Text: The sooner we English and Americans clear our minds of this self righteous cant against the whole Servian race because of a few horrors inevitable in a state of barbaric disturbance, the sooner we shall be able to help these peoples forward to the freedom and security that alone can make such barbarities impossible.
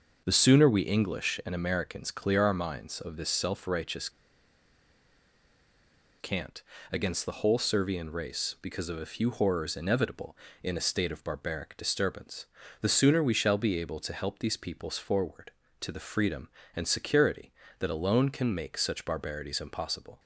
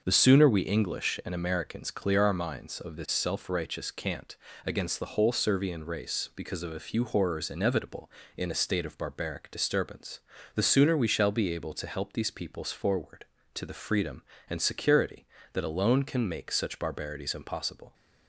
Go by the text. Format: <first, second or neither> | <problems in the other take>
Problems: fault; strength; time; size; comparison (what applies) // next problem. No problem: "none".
second | starts louder than the rest; until 1.2 s; 6 dB; also in the second // pauses between "righteous" and "cant"; strong; at 4.0 s; 2.1 s long // pauses between "cant" and "against"; slight; at 6.6 s; 0.30 s long; slight in the second